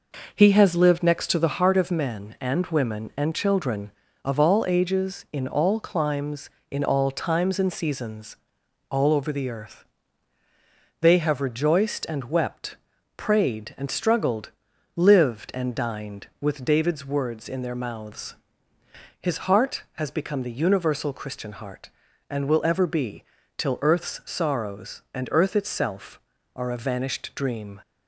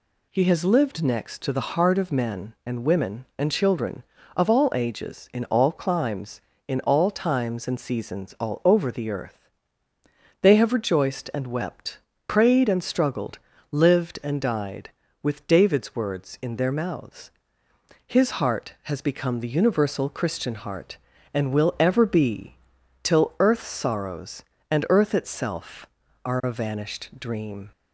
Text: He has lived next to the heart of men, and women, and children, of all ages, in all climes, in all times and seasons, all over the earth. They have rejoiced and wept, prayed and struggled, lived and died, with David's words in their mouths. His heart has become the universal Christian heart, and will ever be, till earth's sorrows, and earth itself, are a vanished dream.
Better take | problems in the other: second | says "dined" for "died"; at 15.7 s

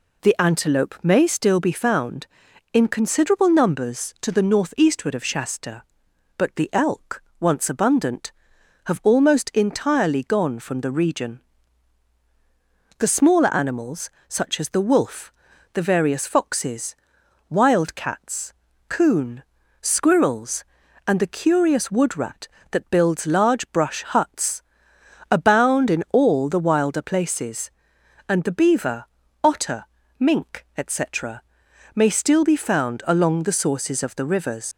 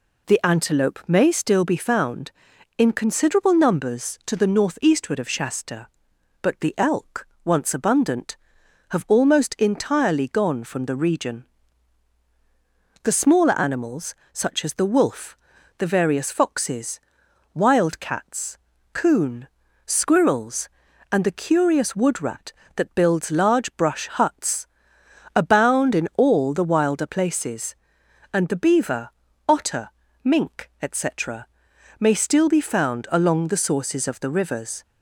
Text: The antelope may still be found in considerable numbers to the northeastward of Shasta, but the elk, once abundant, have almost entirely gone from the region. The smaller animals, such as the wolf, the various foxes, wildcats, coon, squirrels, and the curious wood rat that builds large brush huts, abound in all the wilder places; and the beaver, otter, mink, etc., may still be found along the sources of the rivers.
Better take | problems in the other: second | leaves "rivers" unfinished; at 34.7 s; 80 ms

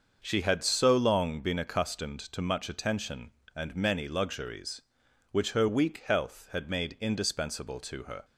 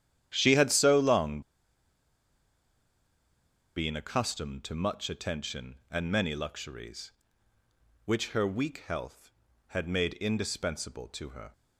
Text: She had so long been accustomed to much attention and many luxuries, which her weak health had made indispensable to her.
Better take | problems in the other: first | starts louder than the rest; strong; until 1.3 s; 10.5 dB; also in the first // pauses between "long" and "been"; strong; at 1.4 s; 2.3 s long

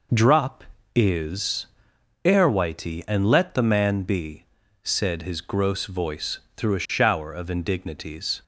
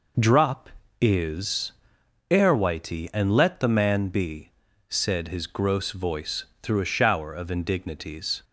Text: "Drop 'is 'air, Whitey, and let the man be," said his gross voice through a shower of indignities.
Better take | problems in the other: neither | pauses between "is" and "air"; noticeable; the same in both // pauses between "voice" and "through"; slight; the same in both

